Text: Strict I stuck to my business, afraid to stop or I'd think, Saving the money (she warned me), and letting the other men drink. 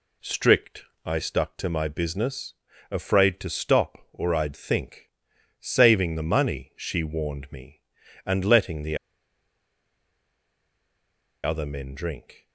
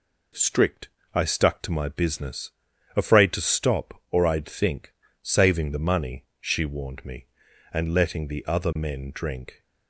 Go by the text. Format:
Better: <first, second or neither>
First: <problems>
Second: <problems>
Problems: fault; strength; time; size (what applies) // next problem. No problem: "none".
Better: second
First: pauses between "Strict" and "I"; slight; at 0.8 s; 0.22 s long // pauses between "the" and "other"; strong; at 8.9 s; 2.4 s long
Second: pauses between "Strict" and "I"; slight; at 0.8 s; 0.26 s long